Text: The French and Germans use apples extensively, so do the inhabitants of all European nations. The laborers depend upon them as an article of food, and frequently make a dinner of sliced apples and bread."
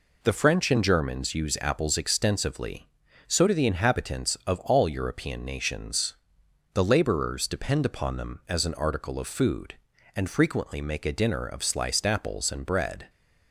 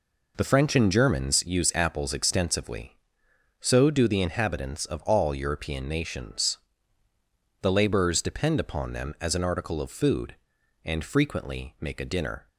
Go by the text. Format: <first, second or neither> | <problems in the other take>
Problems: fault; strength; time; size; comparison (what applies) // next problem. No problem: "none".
first | stops before "of sliced apples and bread"; at 12.4 s